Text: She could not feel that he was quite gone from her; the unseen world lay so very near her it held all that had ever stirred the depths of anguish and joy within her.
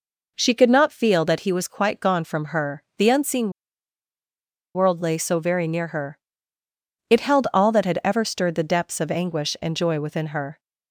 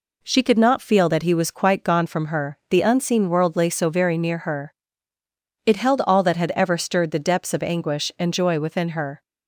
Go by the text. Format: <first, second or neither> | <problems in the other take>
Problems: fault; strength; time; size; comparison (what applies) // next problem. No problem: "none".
second | pauses between "unseen" and "world"; at 3.5 s; 1.2 s long // pauses between "her" and "it"; noticeable; at 6.1 s; 0.92 s long; noticeable in the second